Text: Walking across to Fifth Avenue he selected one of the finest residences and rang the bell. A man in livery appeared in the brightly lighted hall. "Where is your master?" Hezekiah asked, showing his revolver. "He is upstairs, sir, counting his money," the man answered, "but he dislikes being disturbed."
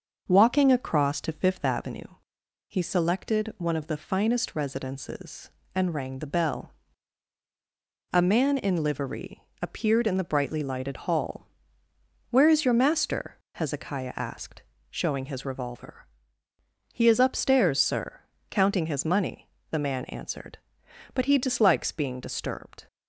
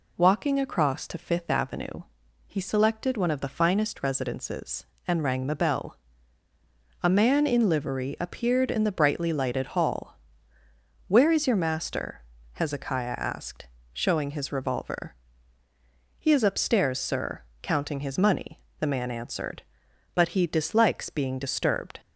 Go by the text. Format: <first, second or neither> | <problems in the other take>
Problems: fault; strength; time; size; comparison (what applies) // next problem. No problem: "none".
second | starts louder than the rest; until 2.0 s; 6 dB // pauses between "Avenue" and "he"; noticeable; at 2.0 s; 0.60 s long; also in the second // pauses between "livery" and "appeared"; slight; at 9.4 s; 0.20 s long